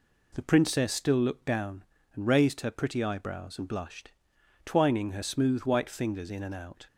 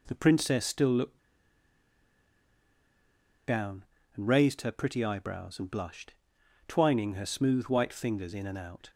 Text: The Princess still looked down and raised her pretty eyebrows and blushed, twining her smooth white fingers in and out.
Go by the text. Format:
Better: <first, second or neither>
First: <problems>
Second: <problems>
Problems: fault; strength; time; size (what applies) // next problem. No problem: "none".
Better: first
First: none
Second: pauses between "looked" and "down"; strong; at 1.1 s; 2.2 s long